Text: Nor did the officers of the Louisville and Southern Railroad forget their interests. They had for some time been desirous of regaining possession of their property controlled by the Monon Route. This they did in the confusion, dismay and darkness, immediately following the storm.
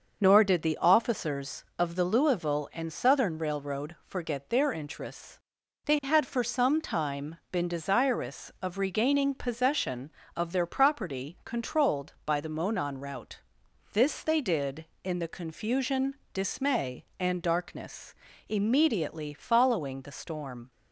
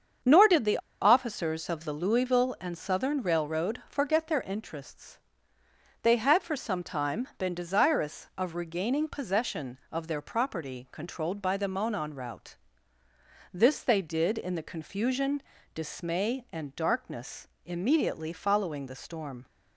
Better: first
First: starts louder than the rest; until 1.2 s; 6 dB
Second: starts louder than the rest; strong; until 1.4 s; 7 dB // pauses between "the" and "officers"; slight; at 0.7 s; 0.23 s long

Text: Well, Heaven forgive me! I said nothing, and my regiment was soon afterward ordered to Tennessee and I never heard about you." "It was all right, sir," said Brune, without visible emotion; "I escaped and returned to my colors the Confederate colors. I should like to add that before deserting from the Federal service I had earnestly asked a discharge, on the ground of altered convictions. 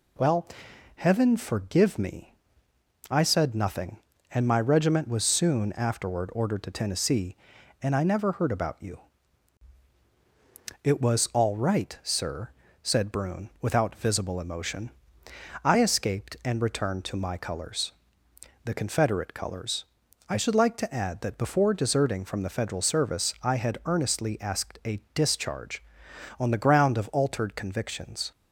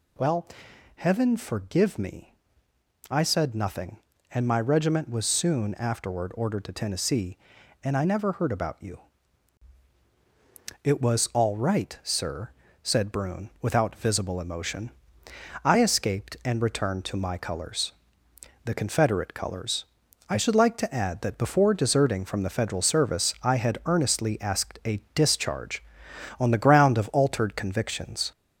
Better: first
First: pauses between "colors" and "the"; noticeable; at 17.9 s; 0.72 s long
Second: gets louder; slight; throughout; 3 dB // pauses between "colors" and "the"; noticeable; at 17.9 s; 0.72 s long

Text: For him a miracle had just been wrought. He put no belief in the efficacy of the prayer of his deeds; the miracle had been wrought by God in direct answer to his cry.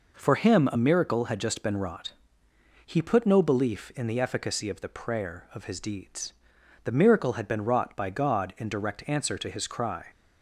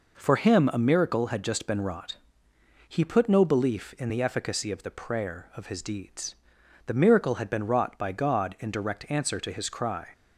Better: neither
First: none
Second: none

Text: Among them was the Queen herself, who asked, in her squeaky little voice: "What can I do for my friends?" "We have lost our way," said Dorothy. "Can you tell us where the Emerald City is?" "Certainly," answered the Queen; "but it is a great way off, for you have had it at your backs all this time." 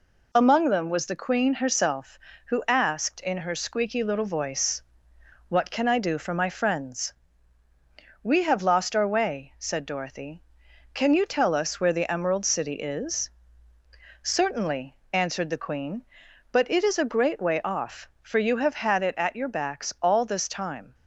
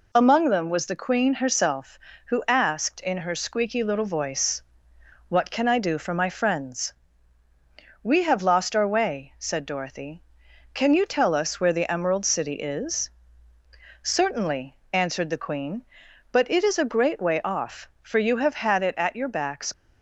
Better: first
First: none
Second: stops before "all this time"; at 19.7 s

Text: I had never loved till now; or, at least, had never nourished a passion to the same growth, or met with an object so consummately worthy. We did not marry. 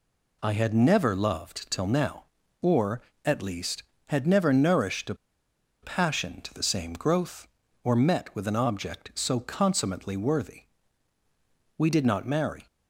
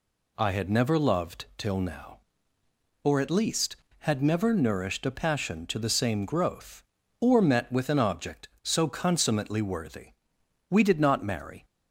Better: second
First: pauses between "a" and "passion"; noticeable; at 5.1 s; 0.67 s long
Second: none

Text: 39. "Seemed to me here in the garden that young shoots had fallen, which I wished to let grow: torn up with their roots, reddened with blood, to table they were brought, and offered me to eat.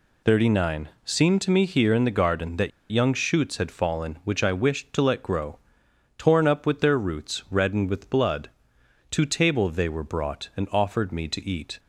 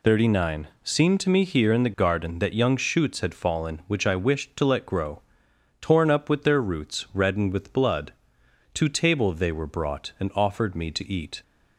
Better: second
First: pauses between "that" and "young"; slight; at 2.7 s; 0.20 s long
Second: none

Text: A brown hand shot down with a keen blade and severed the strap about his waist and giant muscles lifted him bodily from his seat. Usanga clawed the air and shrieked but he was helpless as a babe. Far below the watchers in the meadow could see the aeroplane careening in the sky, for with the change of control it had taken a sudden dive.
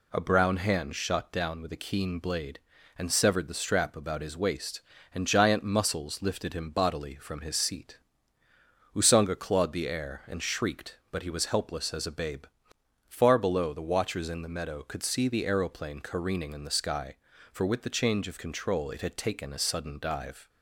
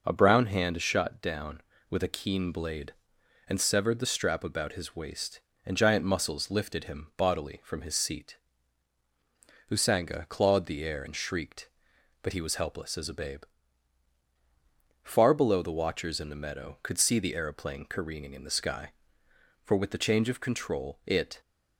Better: first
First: none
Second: stops before "had taken a sudden dive"; at 21.4 s

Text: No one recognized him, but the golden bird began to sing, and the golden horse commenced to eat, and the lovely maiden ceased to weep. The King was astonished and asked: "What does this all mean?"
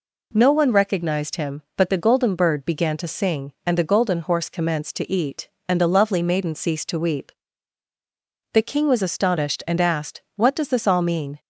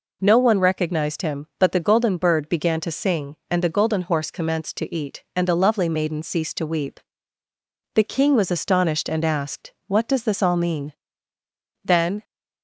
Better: first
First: none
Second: goes on to say "Then"; slight; from 11.8 s on; 0.38 s long

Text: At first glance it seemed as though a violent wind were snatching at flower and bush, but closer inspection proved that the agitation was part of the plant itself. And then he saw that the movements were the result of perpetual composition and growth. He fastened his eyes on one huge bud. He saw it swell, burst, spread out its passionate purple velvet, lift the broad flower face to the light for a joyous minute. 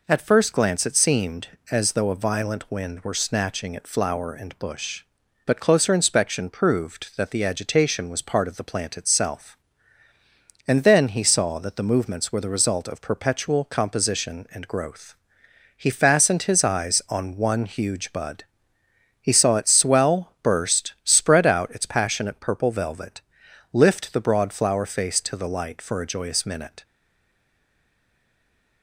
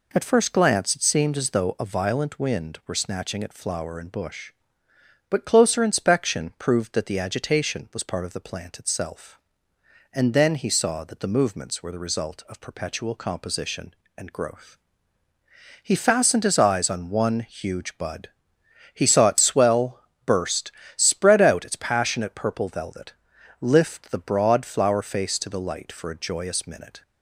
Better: second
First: stays silent after the last word; noticeable; from 26.8 s on; 2.0 s long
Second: none

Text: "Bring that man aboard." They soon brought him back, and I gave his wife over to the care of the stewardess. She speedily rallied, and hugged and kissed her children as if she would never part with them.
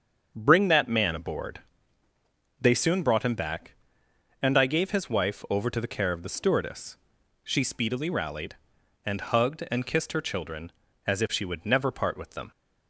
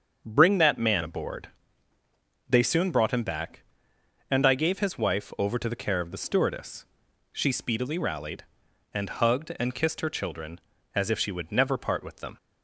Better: neither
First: starts louder than the rest; until 1.3 s; 7 dB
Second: starts louder than the rest; until 1.2 s; 7 dB

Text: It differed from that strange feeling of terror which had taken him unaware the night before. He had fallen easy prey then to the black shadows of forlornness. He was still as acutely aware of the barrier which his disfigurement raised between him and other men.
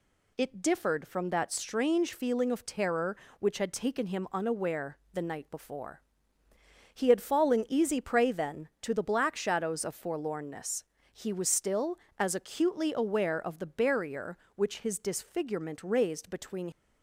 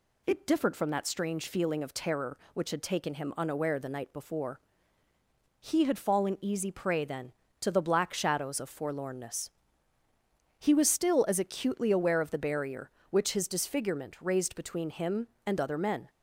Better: second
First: pauses between "unaware" and "the"; slight; at 4.9 s; 0.16 s long // stops before "him and other men"; at 16.7 s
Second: none

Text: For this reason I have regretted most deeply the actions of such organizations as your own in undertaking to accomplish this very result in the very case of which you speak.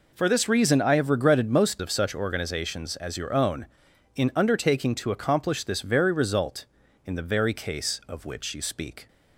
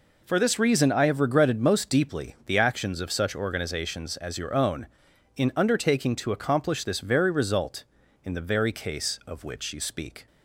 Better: second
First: skips "deeply the actions"; at 1.8 s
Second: none

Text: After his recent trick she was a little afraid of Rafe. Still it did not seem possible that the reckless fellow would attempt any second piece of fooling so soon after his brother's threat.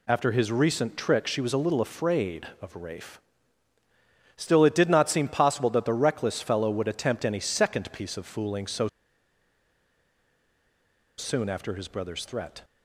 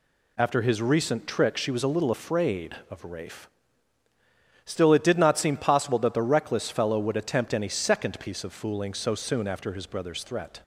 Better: second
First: pauses between "so" and "soon"; strong; at 8.8 s; 2.3 s long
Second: none

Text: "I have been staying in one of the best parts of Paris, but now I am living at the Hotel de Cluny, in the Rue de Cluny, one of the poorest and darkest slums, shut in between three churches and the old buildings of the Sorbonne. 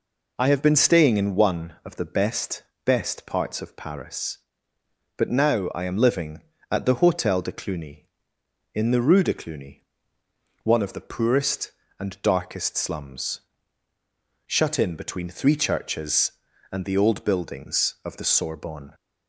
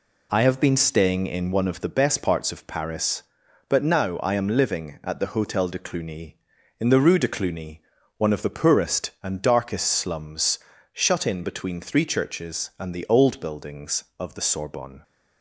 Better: second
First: says "best" twice; at 2.8 s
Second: none

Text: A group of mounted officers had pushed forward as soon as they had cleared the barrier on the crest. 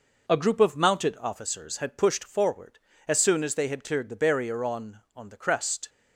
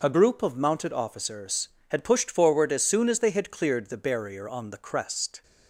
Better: second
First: says "on" twice; at 5.1 s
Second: none

